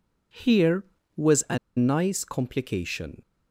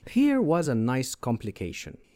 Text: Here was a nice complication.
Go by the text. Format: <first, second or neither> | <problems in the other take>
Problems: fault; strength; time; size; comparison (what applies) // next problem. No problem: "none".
second | pauses between "a" and "nice"; slight; at 1.5 s; 0.19 s long